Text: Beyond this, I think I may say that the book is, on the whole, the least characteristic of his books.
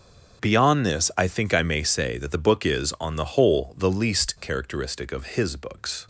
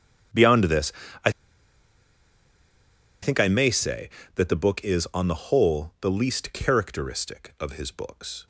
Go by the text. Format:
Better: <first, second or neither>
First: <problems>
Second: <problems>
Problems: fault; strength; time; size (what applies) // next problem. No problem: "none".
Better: first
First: starts louder than the rest; until 1.4 s; 7 dB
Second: starts louder than the rest; strong; until 3.5 s; 9 dB // pauses between "I" and "think"; strong; at 1.3 s; 1.9 s long